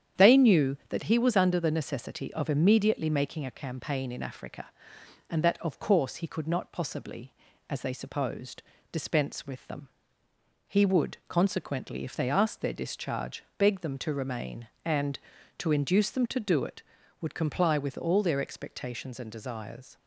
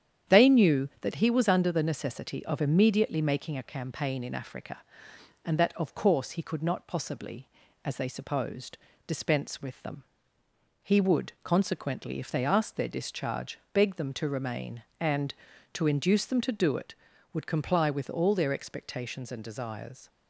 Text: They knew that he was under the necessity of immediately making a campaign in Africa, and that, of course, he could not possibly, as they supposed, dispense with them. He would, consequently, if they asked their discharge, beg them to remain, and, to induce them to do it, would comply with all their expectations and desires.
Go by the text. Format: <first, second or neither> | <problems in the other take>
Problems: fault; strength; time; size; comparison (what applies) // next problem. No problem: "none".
neither | starts louder than the rest; strong; the same in both